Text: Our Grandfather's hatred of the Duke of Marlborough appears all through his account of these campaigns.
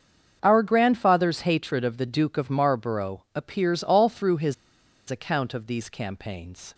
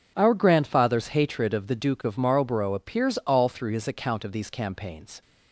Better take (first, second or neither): second